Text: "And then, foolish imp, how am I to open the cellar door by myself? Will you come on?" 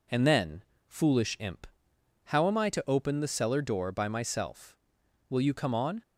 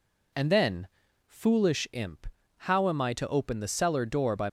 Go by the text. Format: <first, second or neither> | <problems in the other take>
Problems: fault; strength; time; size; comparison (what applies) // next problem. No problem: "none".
first | stops before "myself Will you come on"; at 4.4 s